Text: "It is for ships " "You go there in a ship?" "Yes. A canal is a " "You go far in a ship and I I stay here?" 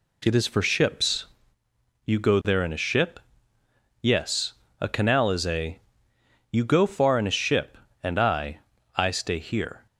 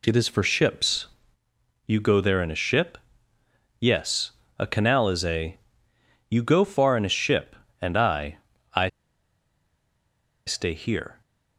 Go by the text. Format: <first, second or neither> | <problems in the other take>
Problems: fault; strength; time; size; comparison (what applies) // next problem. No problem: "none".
first | pauses between "I" and "I"; at 8.3 s; 0.38 s long; also in the first // pauses between "I" and "stay"; strong; at 8.8 s; 1.5 s long